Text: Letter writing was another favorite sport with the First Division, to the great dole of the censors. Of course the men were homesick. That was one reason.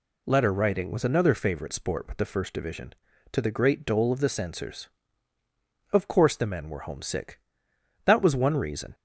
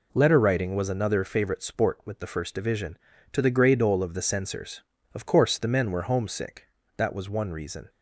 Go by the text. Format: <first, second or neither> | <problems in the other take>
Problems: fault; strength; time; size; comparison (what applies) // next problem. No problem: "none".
first | says "grey" for "great"; at 3.5 s